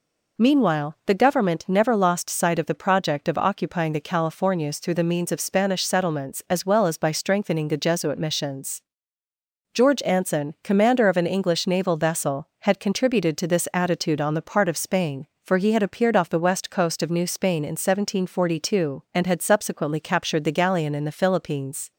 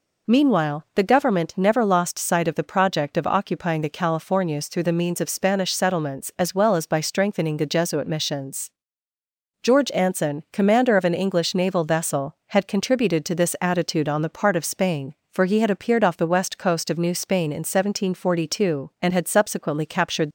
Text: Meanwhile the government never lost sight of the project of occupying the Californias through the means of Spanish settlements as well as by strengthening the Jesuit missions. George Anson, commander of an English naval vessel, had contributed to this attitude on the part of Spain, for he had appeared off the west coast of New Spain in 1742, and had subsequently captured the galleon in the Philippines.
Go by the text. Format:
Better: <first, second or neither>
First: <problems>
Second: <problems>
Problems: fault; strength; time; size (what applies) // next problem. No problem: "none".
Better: first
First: none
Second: stops before "the galleon in the Philippines"; at 20.2 s